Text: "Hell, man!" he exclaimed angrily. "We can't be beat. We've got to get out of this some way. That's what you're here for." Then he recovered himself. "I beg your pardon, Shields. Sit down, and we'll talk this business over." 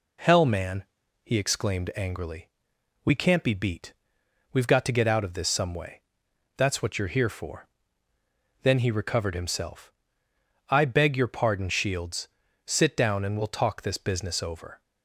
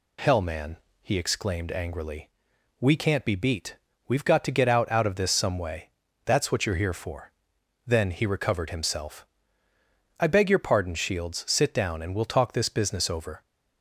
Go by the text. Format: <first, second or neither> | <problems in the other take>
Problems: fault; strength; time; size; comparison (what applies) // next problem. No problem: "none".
first | says "out" twice; at 4.9 s